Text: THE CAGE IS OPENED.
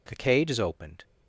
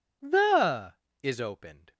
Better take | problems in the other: first | skips "CAGE"; at 1.0 s

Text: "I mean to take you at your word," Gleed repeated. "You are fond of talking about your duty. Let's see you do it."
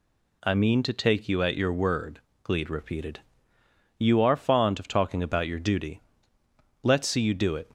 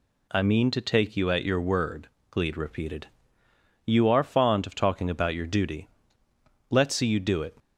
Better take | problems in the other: neither | none

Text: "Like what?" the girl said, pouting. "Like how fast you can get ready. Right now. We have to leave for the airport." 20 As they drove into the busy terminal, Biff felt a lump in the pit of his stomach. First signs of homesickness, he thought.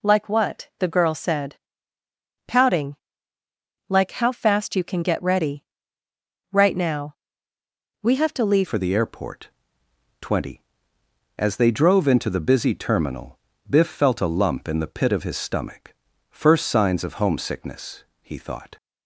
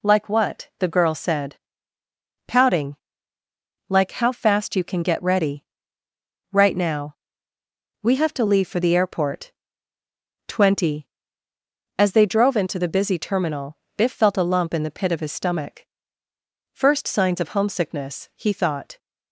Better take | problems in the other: second | changes voice at "for"; from 8.6 s on; 10.1 s long

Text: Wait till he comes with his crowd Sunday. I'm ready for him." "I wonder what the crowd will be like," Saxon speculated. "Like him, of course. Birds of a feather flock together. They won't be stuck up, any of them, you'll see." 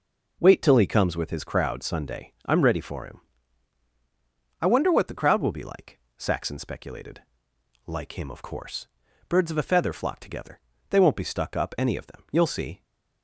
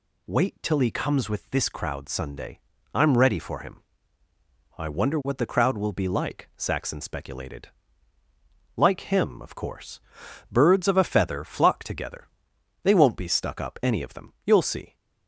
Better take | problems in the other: first | says "this" for "his"; at 1.4 s

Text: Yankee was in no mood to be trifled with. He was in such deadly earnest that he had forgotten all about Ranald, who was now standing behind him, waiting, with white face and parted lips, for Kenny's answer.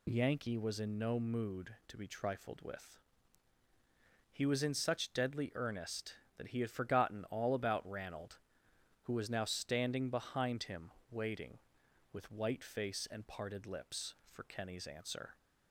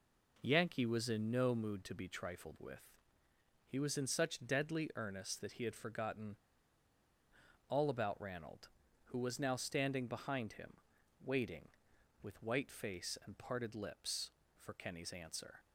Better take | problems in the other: first | pauses between "forgotten" and "all"; strong; at 6.3 s; 1.3 s long

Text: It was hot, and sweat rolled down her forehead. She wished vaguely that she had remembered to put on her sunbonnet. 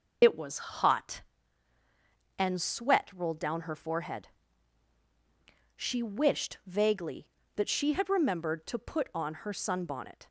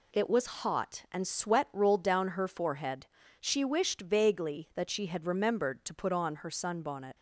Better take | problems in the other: second | loses the start of "It"; at 0.2 s; 50 ms

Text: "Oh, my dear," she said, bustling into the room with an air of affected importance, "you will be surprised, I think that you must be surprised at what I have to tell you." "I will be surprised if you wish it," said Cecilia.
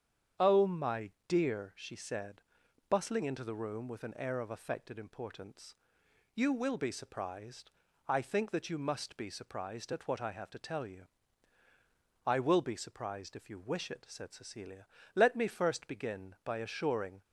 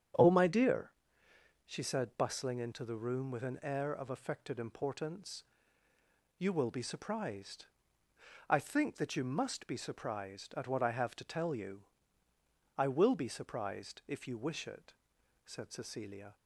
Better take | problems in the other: second | starts louder than the rest; strong; until 1.5 s; 8.5 dB; strong in the second // pauses between "my" and "dear"; slight; at 1.1 s; 0.18 s long // goes on to say "Let me first begin by assuring"; strong; from 15.1 s on; 2.0 s long

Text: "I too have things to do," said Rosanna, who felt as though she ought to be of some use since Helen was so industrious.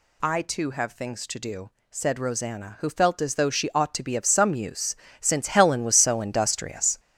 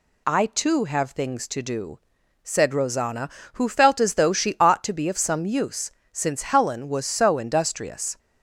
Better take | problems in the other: second | gets louder; strong; throughout; 8.5 dB // pauses between "use" and "since"; slight; at 4.9 s; 0.24 s long; slight in the second

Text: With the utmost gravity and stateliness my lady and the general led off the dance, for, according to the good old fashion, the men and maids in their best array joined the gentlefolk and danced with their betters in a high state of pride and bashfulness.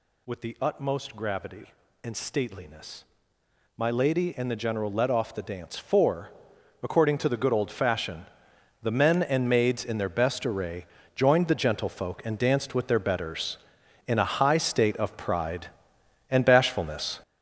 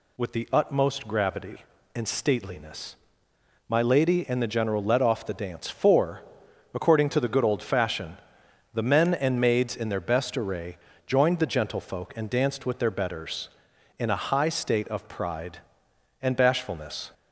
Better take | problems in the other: second | gets louder; strong; throughout; 8.5 dB // pauses between "stateliness" and "my"; noticeable; at 3.0 s; 0.74 s long; noticeable in the second // pauses between "array" and "joined"; slight; at 10.8 s; 0.30 s long; slight in the second

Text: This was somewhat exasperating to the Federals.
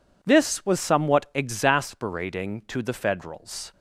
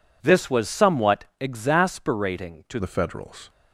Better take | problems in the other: first | pauses between "somewhat" and "exasperating"; slight; at 1.2 s; 0.16 s long // changes voice at "the"; from 2.7 s on; 0.7 s long

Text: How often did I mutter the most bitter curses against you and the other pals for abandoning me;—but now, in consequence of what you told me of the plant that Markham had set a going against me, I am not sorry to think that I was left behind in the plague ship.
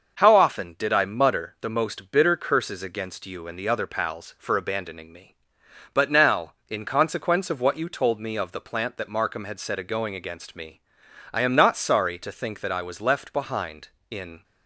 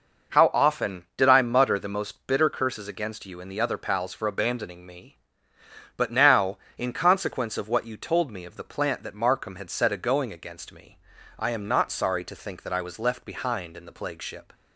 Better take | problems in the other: second | starts louder than the rest; noticeable; until 1.2 s; 6 dB // stops before "the plague ship"; at 14.4 s

